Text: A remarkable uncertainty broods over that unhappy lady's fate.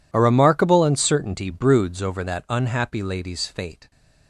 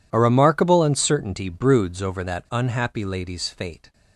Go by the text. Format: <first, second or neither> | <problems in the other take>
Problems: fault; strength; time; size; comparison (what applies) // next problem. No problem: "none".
neither | none